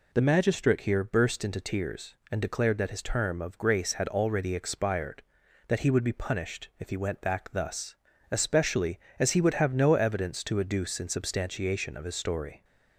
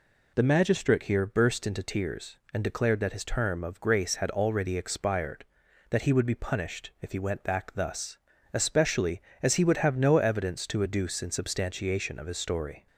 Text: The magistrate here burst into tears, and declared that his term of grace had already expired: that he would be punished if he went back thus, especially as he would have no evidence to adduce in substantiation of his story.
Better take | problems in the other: neither | none

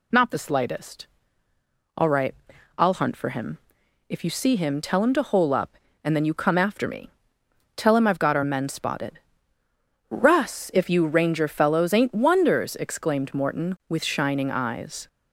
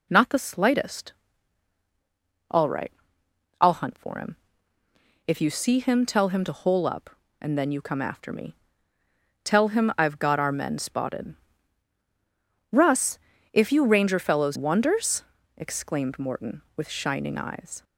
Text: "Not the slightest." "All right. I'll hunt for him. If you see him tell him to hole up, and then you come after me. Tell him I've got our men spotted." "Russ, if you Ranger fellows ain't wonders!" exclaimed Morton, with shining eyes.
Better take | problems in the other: first | skips "ain't"; at 14.5 s

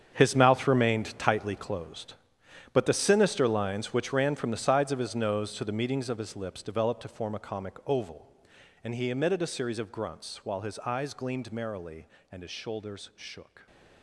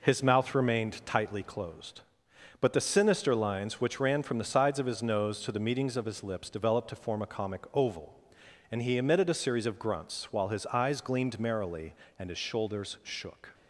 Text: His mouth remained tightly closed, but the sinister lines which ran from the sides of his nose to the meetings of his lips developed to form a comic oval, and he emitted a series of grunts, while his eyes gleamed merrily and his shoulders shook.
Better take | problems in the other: second | gets quieter; strong; throughout; 13.5 dB

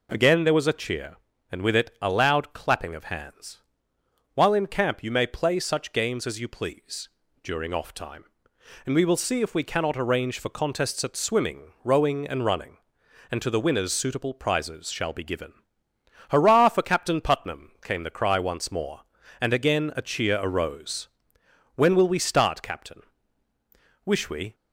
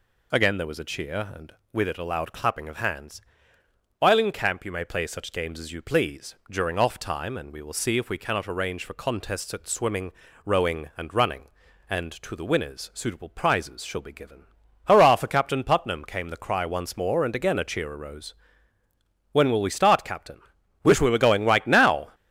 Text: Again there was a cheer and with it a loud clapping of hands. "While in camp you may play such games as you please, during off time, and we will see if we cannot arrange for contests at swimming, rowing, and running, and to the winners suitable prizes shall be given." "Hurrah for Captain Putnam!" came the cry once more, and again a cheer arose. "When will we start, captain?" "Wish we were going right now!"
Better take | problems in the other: second | stops before "were going right now"; at 24.5 s

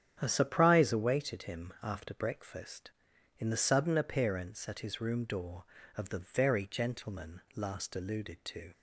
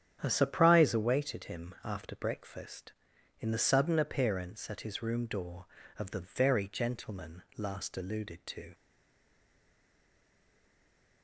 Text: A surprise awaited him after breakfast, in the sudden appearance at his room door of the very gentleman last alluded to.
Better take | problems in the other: first | starts louder than the rest; strong; until 1.2 s; 9.5 dB; strong in the first // stays silent after the last word; from 8.7 s on; 2.5 s long

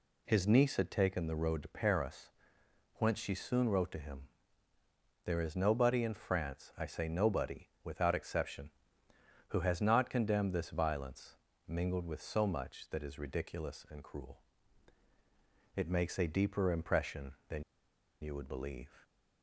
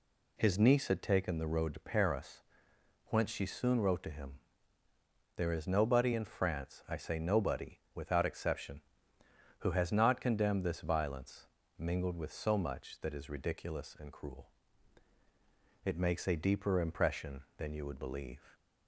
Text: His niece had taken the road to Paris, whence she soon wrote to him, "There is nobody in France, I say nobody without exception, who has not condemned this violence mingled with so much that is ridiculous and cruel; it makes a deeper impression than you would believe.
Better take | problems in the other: second | pauses between "nobody" and "without"; slight; at 7.6 s; 0.16 s long; slight in the second // pauses between "violence" and "mingled"; slight; at 11.3 s; 0.32 s long; slight in the second // pauses between "than" and "you"; noticeable; at 17.6 s; 0.59 s long

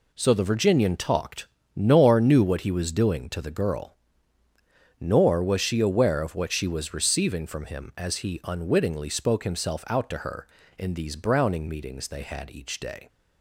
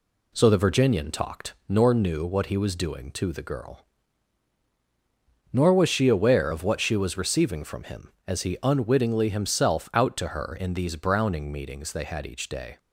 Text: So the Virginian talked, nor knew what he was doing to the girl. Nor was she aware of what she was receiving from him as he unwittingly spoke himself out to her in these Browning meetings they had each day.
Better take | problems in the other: first | skips "spoke"; at 9.2 s

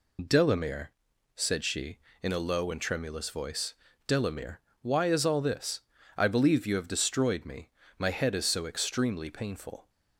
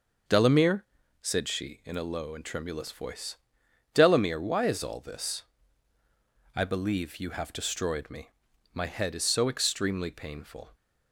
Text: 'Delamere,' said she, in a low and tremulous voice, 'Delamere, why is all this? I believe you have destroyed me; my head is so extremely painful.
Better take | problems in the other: second | loses the start of "Delamere"; at 0.1 s; 40 ms

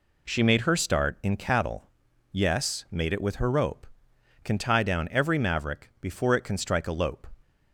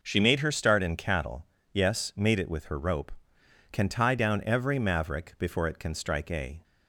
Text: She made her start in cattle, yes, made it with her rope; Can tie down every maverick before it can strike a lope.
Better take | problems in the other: first | stops before "lope"; at 6.6 s

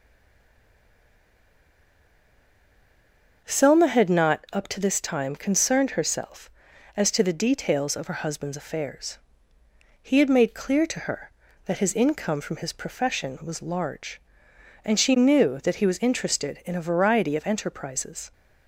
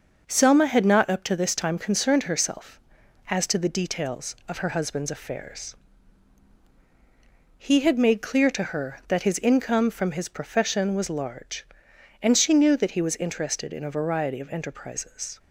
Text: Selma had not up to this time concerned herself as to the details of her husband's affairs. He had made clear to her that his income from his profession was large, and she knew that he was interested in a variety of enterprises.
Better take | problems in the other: second | stays silent before the first word; strong; until 3.4 s; 3.4 s long // starts louder than the rest; until 4.4 s; 6.5 dB; noticeable in the second

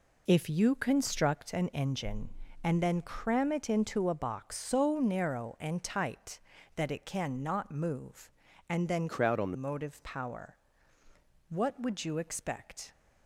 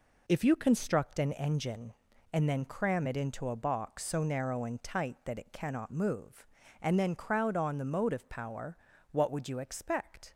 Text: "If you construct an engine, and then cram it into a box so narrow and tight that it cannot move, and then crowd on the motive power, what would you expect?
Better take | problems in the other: second | changes voice from "crowd" to "the"; from 9.0 to 9.5 s; 0.5 s long

